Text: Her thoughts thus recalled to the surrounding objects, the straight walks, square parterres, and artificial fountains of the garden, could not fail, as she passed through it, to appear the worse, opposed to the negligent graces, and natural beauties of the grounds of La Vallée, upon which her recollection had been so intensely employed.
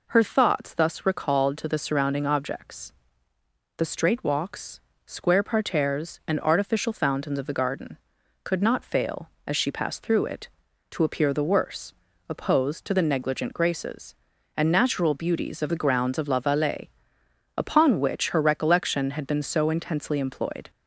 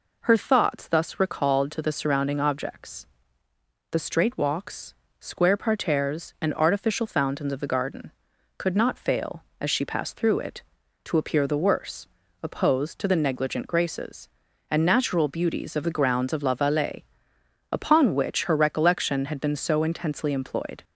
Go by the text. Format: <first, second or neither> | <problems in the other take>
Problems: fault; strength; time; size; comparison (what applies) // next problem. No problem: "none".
neither | none